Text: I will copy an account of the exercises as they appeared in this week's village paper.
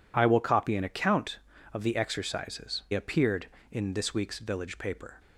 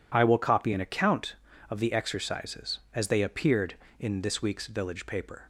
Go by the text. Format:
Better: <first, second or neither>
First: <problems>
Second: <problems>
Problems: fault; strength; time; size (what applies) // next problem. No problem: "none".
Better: second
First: skips "as they"; at 2.8 s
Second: none